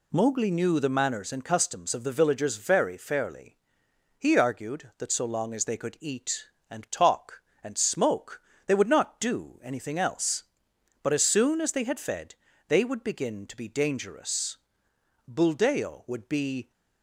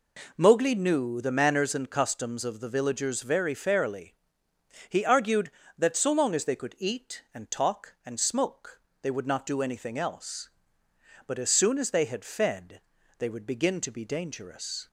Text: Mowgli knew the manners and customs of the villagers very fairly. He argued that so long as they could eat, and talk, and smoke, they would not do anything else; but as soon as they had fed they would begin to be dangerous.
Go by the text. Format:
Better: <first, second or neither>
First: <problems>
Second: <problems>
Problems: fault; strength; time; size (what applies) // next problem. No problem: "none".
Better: second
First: pauses between "fed" and "they"; slight; at 12.3 s; 0.32 s long // goes on to say "Buldeo would be"; from 15.2 s on; 1.4 s long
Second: pauses between "fed" and "they"; at 12.8 s; 0.38 s long